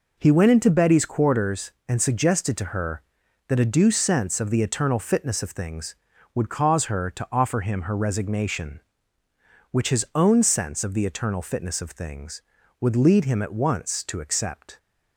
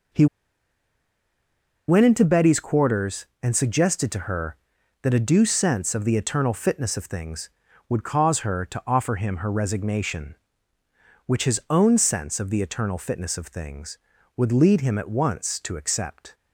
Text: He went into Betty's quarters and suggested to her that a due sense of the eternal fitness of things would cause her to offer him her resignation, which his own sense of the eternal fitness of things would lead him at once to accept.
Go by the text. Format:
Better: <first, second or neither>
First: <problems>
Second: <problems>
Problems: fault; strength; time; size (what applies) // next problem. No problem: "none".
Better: first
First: none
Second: pauses between "He" and "went"; strong; at 0.2 s; 1.6 s long